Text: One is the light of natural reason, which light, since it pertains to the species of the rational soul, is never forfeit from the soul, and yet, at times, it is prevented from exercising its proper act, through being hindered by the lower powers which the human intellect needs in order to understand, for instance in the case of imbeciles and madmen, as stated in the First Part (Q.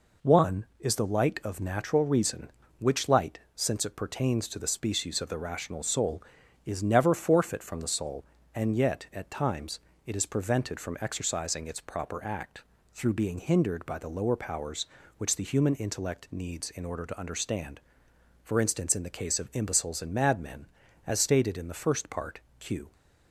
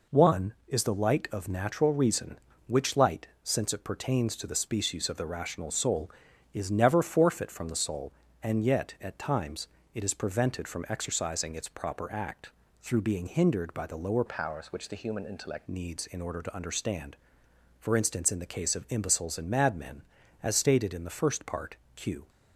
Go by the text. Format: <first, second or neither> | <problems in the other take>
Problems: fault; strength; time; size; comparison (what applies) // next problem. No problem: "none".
first | changes voice from "powers" to "intellect"; from 14.2 to 15.6 s; 1.4 s long